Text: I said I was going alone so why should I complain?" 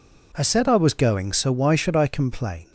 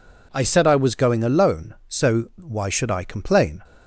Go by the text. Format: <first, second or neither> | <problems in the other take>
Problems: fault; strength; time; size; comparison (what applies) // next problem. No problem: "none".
second | skips "alone"; at 1.3 s